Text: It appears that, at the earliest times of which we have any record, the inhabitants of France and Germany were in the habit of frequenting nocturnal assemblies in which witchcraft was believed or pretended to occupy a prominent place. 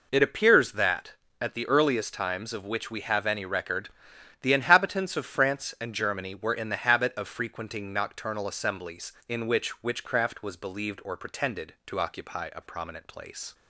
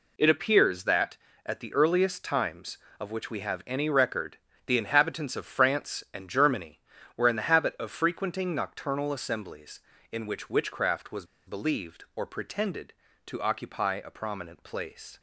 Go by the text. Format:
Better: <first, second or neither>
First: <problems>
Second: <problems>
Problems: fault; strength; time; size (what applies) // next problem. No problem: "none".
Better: first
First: none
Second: pauses between "was" and "believed"; slight; at 11.2 s; 0.21 s long